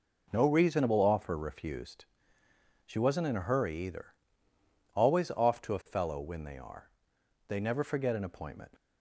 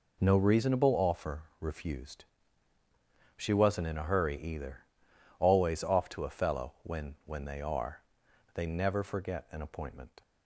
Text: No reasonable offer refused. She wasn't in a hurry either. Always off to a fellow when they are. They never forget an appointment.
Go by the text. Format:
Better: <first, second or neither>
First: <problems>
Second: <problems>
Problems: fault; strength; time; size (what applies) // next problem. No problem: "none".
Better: first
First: none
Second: pauses between "offer" and "refused"; slight; at 1.4 s; 0.18 s long // says "when" twice; at 7.2 s